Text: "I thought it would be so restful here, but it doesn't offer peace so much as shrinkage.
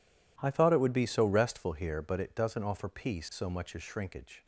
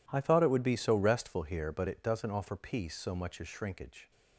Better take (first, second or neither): neither